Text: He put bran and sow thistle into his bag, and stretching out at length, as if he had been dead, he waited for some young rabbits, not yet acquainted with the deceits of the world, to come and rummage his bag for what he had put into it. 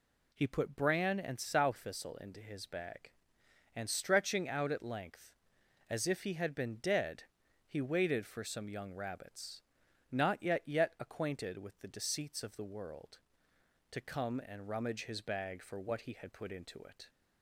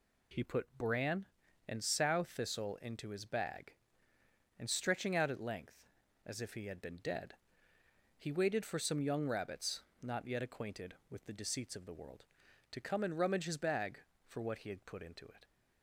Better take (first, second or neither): second